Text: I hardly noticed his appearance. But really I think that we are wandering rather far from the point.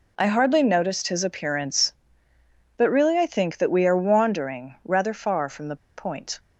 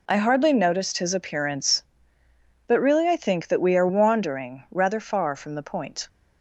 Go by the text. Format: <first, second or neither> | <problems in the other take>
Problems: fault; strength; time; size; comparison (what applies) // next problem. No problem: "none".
second | pauses between "the" and "point"; slight; at 5.7 s; 0.20 s long